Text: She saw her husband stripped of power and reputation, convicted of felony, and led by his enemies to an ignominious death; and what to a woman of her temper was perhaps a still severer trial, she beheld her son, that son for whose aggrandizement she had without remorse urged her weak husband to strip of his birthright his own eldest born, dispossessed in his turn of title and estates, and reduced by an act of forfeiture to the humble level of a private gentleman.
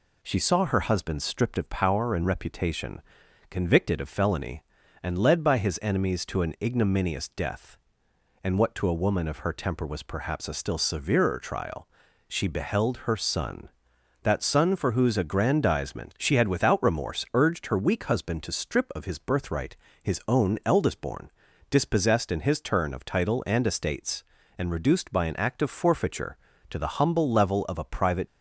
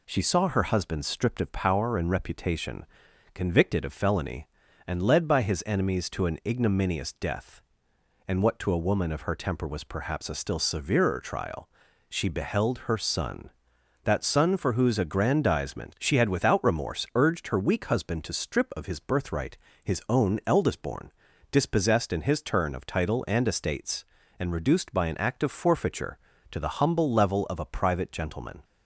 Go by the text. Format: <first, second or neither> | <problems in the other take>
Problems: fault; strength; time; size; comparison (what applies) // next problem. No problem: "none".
second | pauses between "birthright" and "his"; slight; at 19.7 s; 0.28 s long; slight in the second // stops before "gentleman"; at 28.2 s